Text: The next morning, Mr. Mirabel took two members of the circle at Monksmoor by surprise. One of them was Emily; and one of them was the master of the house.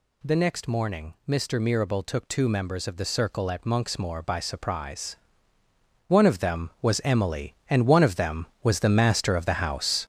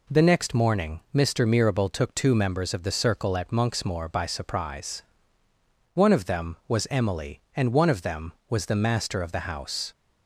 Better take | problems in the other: second | gets louder; strong; throughout; 8.5 dB

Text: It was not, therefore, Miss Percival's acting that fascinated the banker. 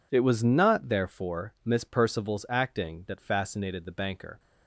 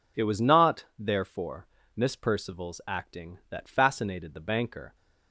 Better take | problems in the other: neither | none

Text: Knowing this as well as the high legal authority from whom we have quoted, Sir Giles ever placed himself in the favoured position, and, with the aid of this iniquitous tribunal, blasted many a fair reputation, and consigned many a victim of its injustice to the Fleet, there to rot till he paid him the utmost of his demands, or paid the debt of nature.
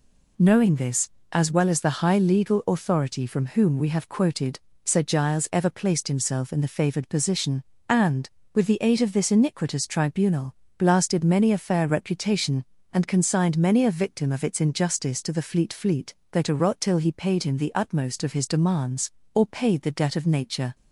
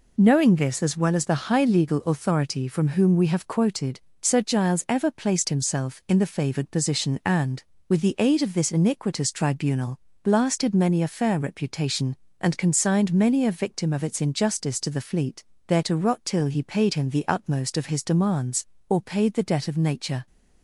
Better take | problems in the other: second | says "Fleet" twice; at 15.7 s

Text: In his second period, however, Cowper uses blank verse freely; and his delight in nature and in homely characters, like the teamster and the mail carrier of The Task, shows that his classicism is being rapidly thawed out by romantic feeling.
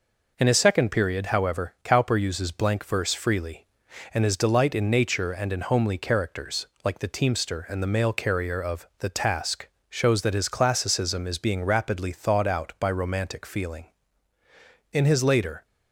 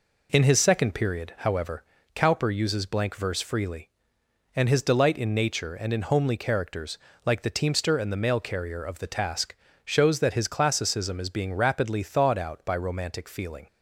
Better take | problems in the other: second | goes on to say "In his later"; noticeable; from 14.9 s on; 0.74 s long

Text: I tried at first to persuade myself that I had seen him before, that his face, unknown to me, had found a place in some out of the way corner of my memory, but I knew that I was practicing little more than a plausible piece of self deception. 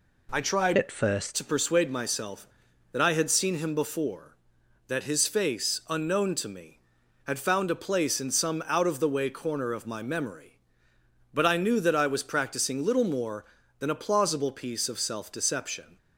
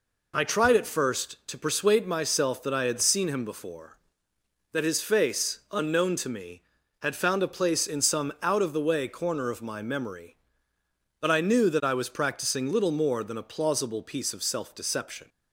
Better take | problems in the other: second | changes voice from "at" to "first"; from 0.7 to 1.3 s; 0.6 s long

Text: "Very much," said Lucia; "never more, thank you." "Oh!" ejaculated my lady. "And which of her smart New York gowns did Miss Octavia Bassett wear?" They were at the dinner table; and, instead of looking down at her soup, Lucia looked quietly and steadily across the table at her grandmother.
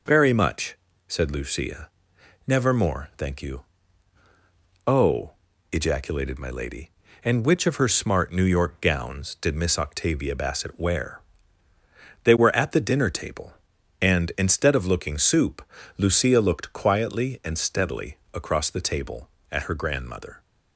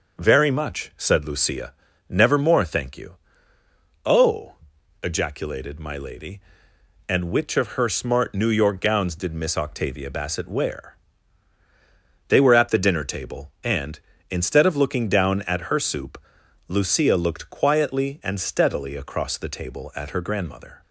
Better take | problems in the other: second | skips "down at her"; at 15.1 s // pauses between "steadily" and "across"; slight; at 18.1 s; 0.16 s long

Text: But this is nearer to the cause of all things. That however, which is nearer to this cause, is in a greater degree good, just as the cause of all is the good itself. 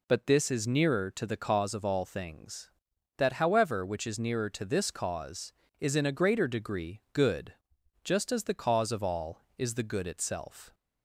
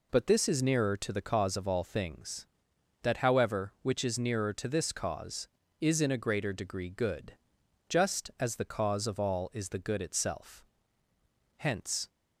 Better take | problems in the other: first | goes on to say "Hence"; from 11.5 s on; 0.52 s long

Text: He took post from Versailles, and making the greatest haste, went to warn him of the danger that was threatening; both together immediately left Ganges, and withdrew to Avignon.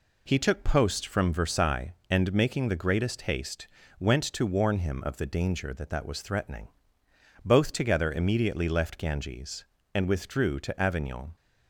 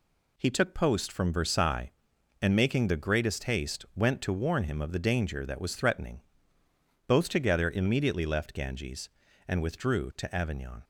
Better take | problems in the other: second | says "that" twice; at 5.9 s

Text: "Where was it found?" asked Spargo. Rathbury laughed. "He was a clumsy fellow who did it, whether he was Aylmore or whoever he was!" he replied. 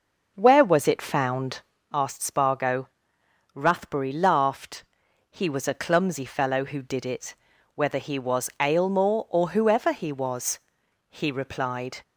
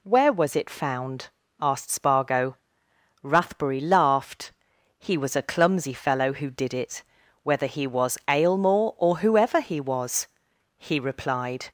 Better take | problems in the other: second | starts louder than the rest; noticeable; until 1.9 s; 6 dB

